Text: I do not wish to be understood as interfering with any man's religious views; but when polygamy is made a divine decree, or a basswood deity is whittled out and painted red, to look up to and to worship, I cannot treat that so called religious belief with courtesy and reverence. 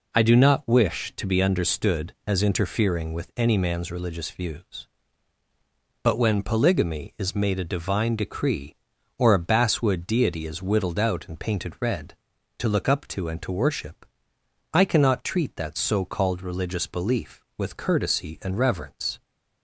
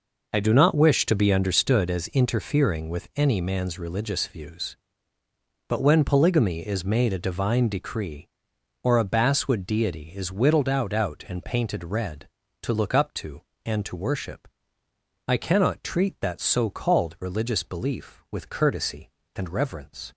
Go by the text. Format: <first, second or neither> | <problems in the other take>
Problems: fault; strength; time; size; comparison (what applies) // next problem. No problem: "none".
first | says "out" twice; at 10.9 s